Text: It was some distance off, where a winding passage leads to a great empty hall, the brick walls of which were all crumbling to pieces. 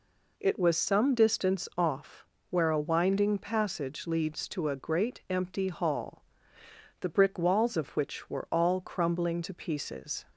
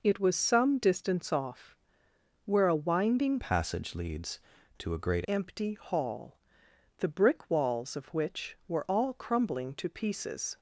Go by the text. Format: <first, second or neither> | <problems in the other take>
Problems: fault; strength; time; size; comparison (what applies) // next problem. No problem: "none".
first | changes voice from "passage" to "great"; from 3.4 to 5.2 s; 1.8 s long